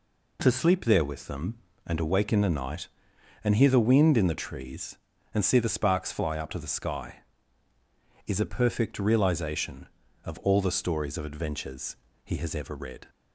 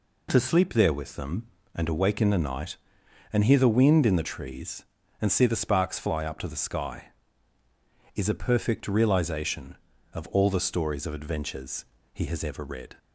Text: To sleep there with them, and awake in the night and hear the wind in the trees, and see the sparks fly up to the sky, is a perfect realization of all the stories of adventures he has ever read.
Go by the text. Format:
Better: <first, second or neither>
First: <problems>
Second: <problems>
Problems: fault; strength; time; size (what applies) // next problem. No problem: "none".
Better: neither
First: pauses between "adventures" and "he"; slight; at 11.9 s; 0.26 s long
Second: pauses between "adventures" and "he"; slight; at 11.8 s; 0.26 s long